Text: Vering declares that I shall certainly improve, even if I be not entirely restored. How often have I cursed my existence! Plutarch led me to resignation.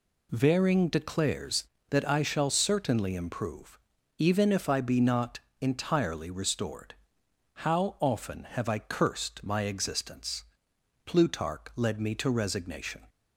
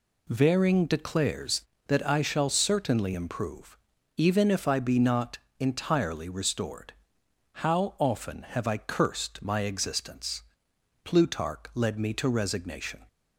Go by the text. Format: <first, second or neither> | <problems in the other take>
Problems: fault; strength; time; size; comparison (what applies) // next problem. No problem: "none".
neither | pauses between "not" and "entirely"; slight; the same in both